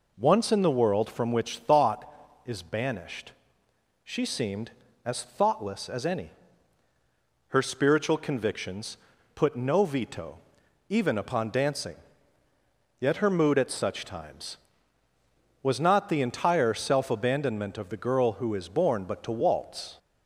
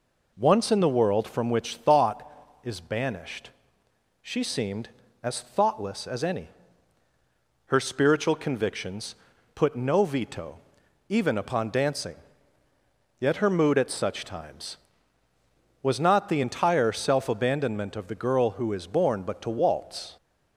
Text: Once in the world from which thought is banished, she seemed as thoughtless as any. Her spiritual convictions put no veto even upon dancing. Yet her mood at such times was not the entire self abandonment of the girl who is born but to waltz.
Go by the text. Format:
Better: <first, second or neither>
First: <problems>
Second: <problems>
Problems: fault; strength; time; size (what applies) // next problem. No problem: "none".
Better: neither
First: pauses between "convictions" and "put"; at 8.9 s; 0.39 s long // pauses between "veto" and "even"; noticeable; at 10.3 s; 0.50 s long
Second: pauses between "convictions" and "put"; at 9.1 s; 0.40 s long // pauses between "veto" and "even"; noticeable; at 10.5 s; 0.50 s long